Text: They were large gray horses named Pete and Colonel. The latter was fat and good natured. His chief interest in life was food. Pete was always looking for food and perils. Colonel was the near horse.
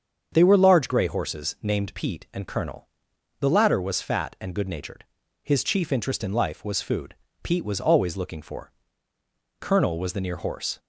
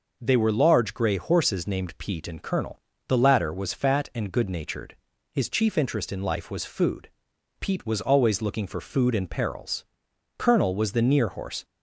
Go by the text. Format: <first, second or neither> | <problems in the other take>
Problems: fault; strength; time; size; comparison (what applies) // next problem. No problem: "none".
second | starts louder than the rest; strong; until 1.3 s; 7 dB // skips "food and perils"; at 9.1 s